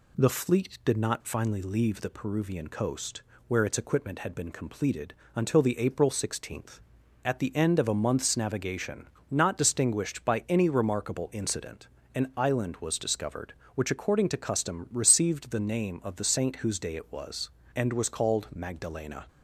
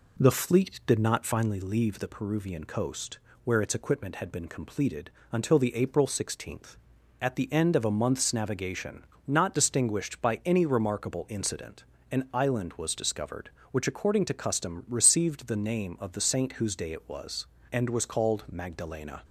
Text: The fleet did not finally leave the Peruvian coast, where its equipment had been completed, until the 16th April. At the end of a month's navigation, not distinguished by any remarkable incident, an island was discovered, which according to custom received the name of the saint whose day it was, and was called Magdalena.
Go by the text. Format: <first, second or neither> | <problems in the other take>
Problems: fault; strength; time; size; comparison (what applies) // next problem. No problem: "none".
first | starts louder than the rest; until 1.5 s; 3.5 dB